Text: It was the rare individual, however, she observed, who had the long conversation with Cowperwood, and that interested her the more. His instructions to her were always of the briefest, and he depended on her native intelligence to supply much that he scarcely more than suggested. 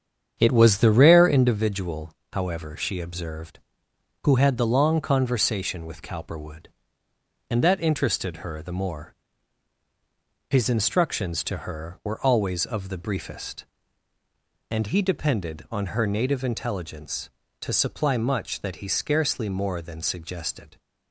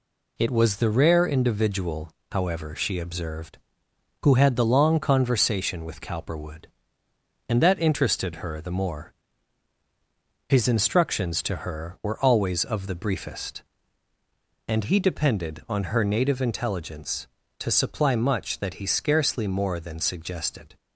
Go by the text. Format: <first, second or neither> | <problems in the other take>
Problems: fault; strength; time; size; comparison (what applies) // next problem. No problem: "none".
second | starts louder than the rest; strong; until 1.7 s; 8 dB